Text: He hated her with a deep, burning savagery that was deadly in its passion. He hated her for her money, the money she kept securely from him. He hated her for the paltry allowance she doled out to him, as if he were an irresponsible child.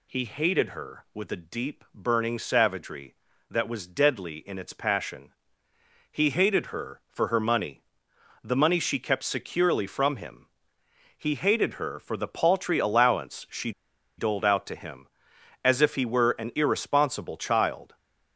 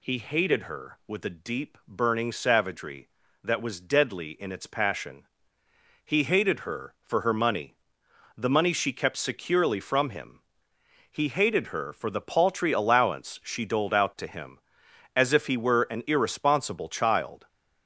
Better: second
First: pauses between "she" and "doled"; noticeable; at 13.7 s; 0.46 s long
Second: none

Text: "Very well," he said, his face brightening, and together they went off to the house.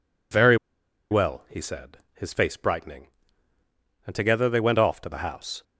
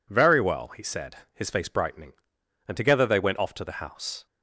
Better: second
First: pauses between "Very" and "well"; noticeable; at 0.5 s; 0.54 s long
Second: none

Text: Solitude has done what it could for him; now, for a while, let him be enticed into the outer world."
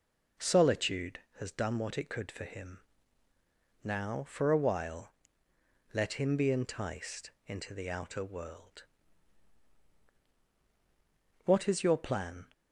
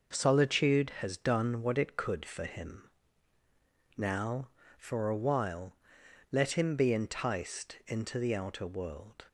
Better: second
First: pauses between "enticed" and "into"; slight; at 7.3 s; 0.16 s long // goes on to say "What is your plan"; noticeable; from 11.4 s on; 1.0 s long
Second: none

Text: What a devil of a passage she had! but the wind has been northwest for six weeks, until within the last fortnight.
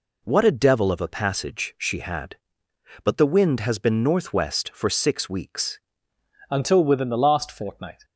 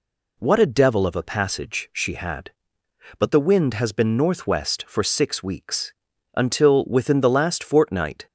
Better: second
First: changes voice at "until"; from 6.4 s on; 1.6 s long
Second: none

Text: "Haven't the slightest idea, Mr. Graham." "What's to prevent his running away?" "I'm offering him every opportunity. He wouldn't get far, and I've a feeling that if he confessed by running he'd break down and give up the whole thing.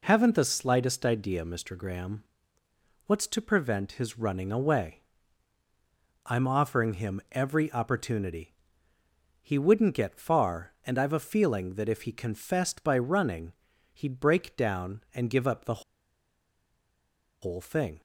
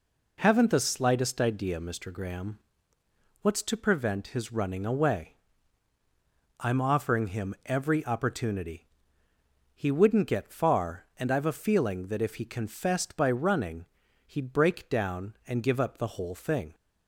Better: second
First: pauses between "running" and "he'd"; at 13.5 s; 0.40 s long // pauses between "the" and "whole"; strong; at 15.8 s; 1.6 s long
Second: pauses between "running" and "he'd"; at 13.8 s; 0.40 s long

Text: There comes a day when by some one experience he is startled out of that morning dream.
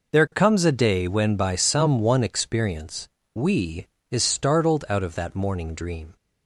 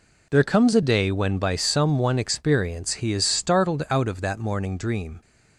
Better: second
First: says "we" for "he"; at 3.3 s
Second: none

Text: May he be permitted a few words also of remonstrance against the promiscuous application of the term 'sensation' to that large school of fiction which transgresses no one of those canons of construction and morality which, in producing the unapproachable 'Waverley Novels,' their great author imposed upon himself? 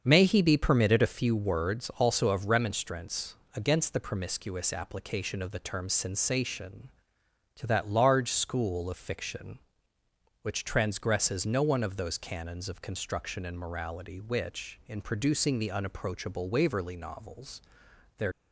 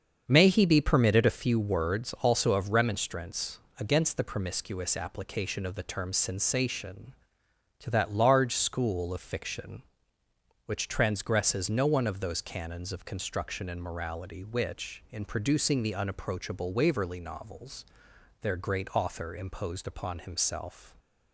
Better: second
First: starts louder than the rest; until 1.0 s; 7 dB // pauses between "remonstrance" and "against"; slight; at 3.3 s; 0.18 s long // stops before "great author imposed upon himself"; at 18.3 s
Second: starts louder than the rest; until 1.2 s; 7 dB // pauses between "remonstrance" and "against"; slight; at 3.5 s; 0.18 s long

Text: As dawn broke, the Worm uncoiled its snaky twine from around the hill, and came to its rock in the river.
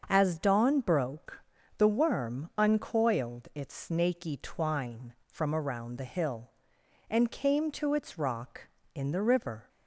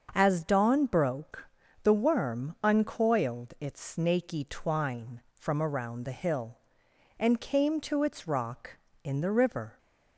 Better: neither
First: starts louder than the rest; until 1.0 s; 6.5 dB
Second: starts louder than the rest; until 1.1 s; 6.5 dB

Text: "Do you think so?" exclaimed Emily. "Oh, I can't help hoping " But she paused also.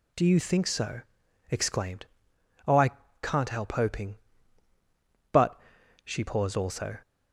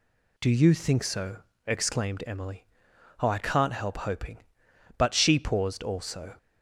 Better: second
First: skips "Emily"; at 2.3 s // pauses between "I" and "can't"; slight; at 2.9 s; 0.32 s long // pauses between "But" and "she"; noticeable; at 5.5 s; 0.46 s long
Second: none

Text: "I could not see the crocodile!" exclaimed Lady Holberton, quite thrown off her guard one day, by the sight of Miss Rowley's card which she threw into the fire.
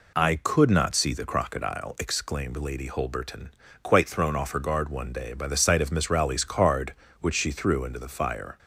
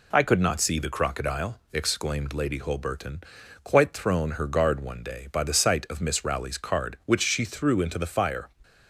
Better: first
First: none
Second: skips "off"; at 4.3 s

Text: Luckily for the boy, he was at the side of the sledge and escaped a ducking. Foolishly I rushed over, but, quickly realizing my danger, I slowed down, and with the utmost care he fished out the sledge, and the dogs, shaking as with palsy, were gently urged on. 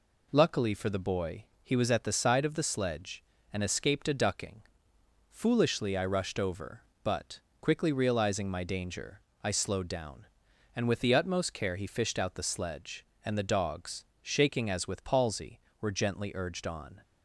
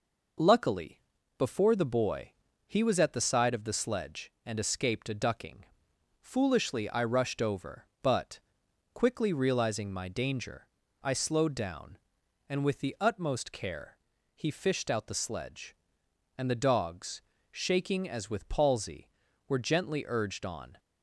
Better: first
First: none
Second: says "before" for "for"; at 1.3 s // pauses between "care" and "he"; at 13.9 s; 0.38 s long

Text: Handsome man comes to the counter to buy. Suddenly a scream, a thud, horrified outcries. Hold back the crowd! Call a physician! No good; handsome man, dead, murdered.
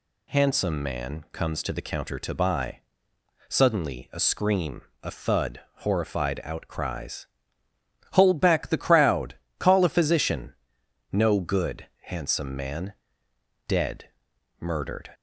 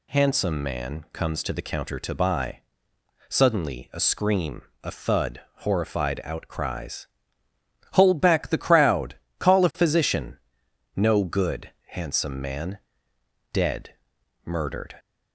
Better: neither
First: none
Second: none

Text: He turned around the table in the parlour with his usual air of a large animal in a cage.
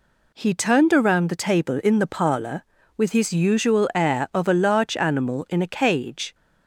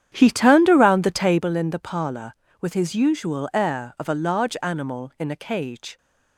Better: first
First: none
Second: starts louder than the rest; strong; until 1.5 s; 9.5 dB

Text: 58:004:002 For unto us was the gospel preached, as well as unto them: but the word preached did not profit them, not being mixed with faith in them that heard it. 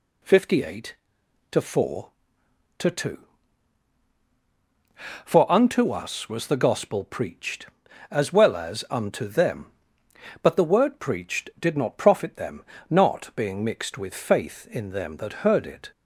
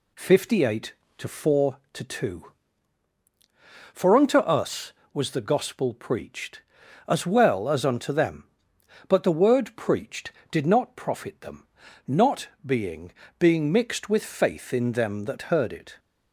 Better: first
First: none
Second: pauses between "not" and "being"; slight; at 12.4 s; 0.18 s long // says "being" twice; at 13.4 s

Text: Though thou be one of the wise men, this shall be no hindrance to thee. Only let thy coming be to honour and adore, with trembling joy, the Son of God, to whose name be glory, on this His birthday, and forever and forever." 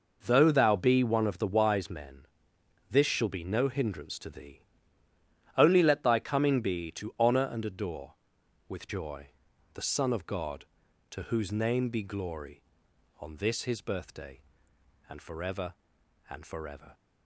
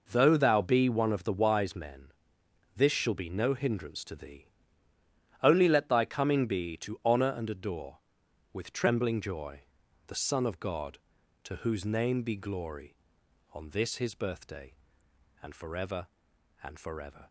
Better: second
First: skips "trembling"; at 8.8 s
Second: none

